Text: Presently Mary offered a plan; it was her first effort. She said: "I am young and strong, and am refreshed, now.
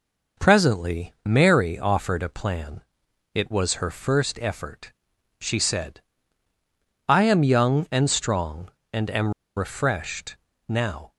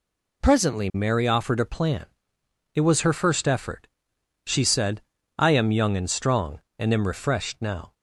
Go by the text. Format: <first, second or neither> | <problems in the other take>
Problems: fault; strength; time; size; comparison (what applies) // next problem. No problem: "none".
second | pauses between "am" and "refreshed"; slight; at 9.3 s; 0.24 s long